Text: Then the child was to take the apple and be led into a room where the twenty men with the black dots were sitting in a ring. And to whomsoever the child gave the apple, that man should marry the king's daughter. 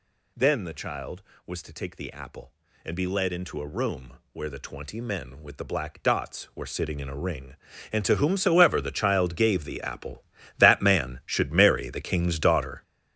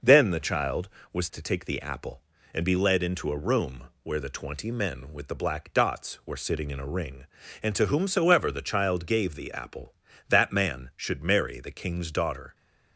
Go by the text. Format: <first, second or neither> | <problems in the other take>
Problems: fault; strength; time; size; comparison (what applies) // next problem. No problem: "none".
second | gets louder; strong; throughout; 10 dB // pauses between "room" and "where"; slight; at 4.1 s; 0.18 s long; slight in the second